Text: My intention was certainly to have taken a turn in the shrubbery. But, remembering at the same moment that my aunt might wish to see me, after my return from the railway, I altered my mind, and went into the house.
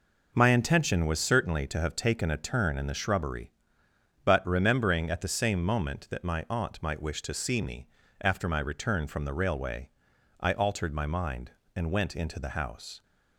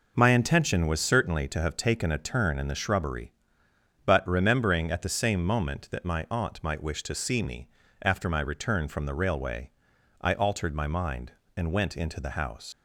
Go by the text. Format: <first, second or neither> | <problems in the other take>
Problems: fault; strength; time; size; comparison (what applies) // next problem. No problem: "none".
first | leaves "house" unfinished; at 12.7 s; 105 ms